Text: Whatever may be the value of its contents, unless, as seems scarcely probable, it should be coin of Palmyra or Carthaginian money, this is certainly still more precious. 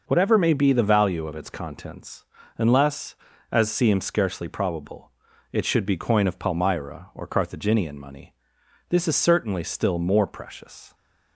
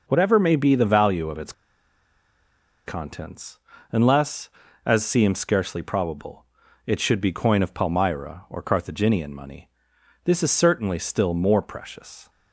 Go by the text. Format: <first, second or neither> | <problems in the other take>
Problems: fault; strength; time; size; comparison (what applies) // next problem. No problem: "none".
first | pauses between "its" and "contents"; strong; at 1.5 s; 1.3 s long